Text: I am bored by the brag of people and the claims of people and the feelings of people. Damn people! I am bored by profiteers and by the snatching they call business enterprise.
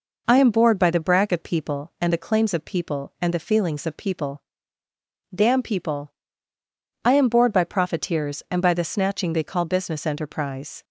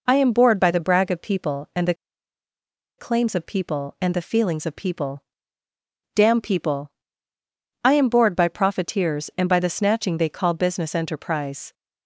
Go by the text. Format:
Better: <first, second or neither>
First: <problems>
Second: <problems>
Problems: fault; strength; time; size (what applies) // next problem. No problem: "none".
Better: first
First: none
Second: pauses between "the" and "claims"; at 1.9 s; 1.0 s long